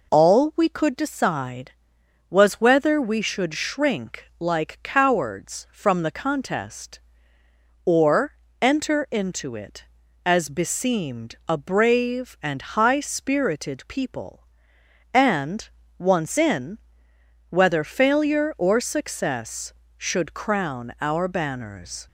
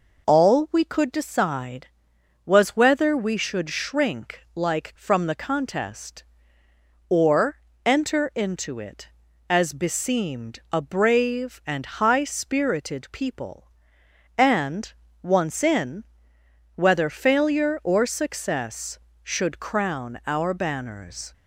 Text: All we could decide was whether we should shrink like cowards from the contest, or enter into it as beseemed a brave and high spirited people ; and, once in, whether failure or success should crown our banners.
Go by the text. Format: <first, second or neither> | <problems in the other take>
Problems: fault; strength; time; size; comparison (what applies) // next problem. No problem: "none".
first | skips "cowards"; at 4.9 s // pauses between "or" and "enter"; slight; at 7.5 s; 0.26 s long; slight in the first